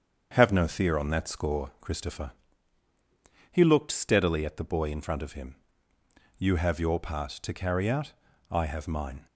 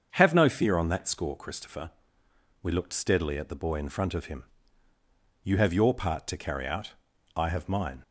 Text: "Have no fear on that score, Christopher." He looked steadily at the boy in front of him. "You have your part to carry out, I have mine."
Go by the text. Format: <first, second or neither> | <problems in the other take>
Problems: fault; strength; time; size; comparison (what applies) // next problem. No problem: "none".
first | starts louder than the rest; until 1.1 s; 7 dB; also in the first // says "We" for "He"; at 2.6 s